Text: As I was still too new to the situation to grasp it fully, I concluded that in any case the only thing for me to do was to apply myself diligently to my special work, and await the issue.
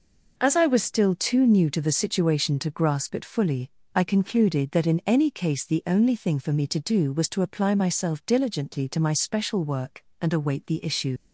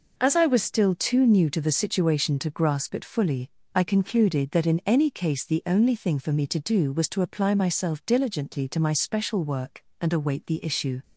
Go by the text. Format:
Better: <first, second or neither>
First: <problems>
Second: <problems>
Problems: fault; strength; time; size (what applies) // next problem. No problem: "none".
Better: second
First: leaves "issue" unfinished; at 11.1 s; 60 ms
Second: none